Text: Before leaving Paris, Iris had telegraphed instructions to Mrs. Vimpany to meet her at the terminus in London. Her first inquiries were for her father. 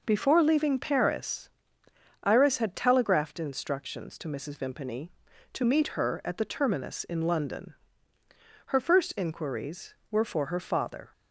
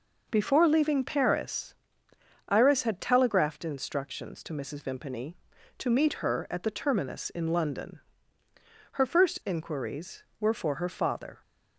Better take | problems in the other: neither | none

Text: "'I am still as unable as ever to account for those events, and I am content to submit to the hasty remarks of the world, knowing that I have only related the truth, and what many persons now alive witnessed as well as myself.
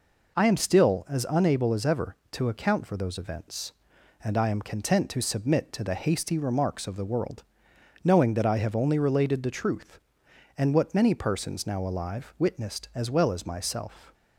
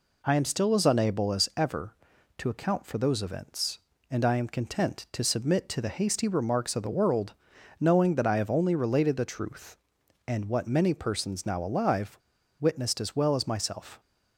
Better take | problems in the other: first | pauses between "alive" and "witnessed"; at 12.1 s; 0.42 s long

